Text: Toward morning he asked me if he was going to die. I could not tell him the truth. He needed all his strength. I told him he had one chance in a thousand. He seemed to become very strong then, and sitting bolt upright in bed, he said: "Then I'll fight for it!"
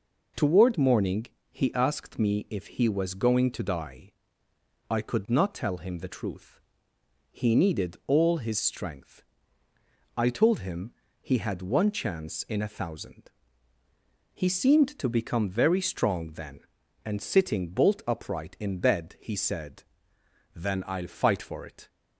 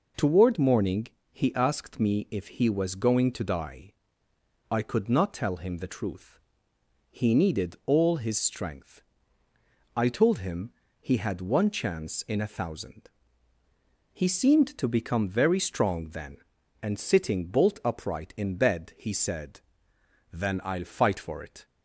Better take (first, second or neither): neither